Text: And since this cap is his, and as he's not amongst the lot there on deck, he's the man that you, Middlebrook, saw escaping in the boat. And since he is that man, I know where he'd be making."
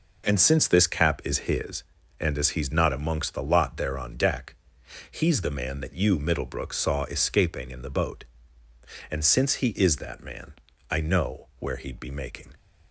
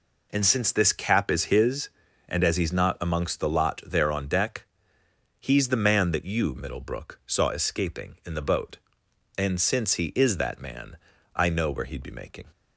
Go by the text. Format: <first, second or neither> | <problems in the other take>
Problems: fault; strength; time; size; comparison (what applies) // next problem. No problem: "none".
neither | none